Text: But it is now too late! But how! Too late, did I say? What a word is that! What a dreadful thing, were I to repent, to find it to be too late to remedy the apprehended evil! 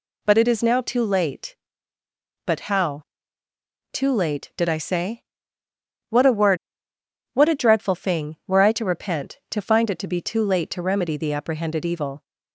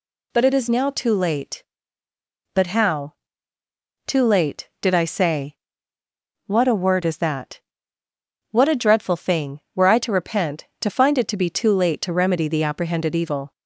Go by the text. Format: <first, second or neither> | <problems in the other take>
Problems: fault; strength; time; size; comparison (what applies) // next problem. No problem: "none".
second | skips "is that"; at 6.9 s